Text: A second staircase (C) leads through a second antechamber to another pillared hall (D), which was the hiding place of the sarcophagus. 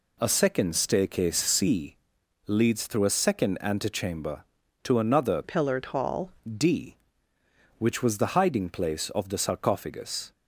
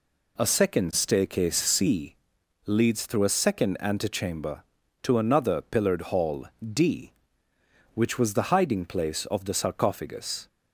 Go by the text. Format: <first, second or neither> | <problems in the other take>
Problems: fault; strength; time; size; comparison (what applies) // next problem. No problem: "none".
second | changes voice from "pillared" to "hall"; from 5.4 to 6.3 s; 0.9 s long